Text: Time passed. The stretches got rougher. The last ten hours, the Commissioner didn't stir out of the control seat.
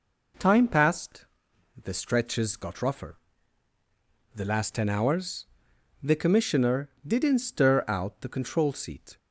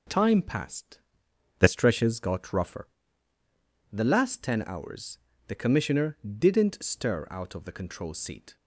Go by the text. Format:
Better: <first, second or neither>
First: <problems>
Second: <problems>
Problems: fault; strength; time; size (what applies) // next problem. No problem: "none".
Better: second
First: pauses between "Commissioner" and "didn't"; slight; at 6.8 s; 0.16 s long // skips "of"; at 8.1 s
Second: pauses between "Commissioner" and "didn't"; slight; at 6.1 s; 0.24 s long